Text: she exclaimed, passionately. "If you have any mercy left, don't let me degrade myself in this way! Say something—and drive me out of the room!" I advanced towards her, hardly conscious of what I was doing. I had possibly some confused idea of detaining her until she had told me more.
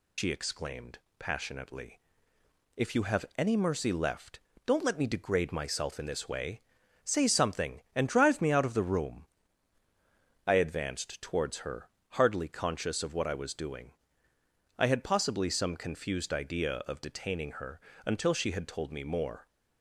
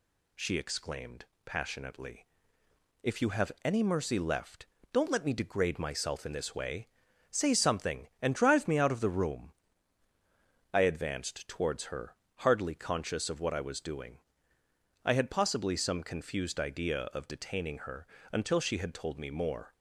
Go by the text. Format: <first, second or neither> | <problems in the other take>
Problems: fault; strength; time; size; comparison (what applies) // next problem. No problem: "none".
second | loses the start of "she"; at 0.1 s; 95 ms // pauses between "her" and "until"; slight; at 17.8 s; 0.26 s long; slight in the second